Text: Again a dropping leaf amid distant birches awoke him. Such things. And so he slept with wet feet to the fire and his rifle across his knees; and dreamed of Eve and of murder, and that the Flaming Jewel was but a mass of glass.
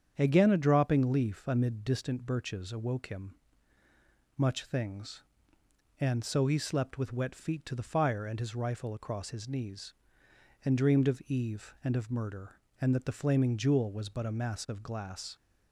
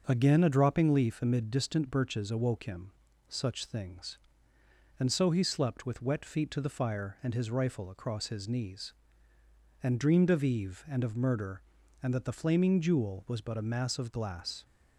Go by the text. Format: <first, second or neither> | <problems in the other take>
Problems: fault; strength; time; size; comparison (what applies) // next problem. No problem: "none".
second | starts louder than the rest; strong; until 1.1 s; 8 dB; also in the second // says "Much" for "Such"; at 4.3 s